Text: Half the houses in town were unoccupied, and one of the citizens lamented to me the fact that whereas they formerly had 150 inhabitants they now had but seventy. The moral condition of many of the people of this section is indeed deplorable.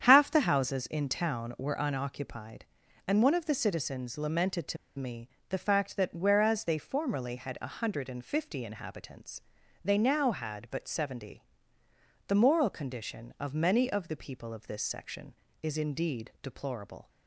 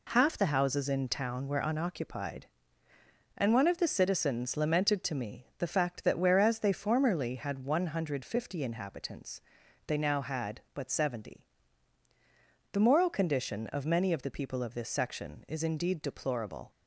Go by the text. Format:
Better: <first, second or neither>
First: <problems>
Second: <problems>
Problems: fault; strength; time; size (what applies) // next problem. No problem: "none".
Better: second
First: starts louder than the rest; strong; until 1.0 s; 8.5 dB // pauses between "to" and "me"; slight; at 4.7 s; 0.22 s long // pauses between "me" and "the"; slight; at 5.3 s; 0.18 s long // pauses between "inhabitants" and "they"; at 9.4 s; 0.42 s long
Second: pauses between "inhabitants" and "they"; noticeable; at 9.3 s; 0.48 s long